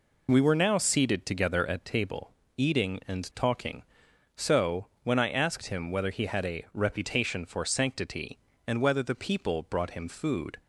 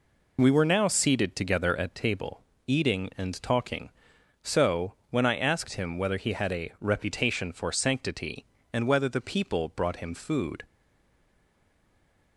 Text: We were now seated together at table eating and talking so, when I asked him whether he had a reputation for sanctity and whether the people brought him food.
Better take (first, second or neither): first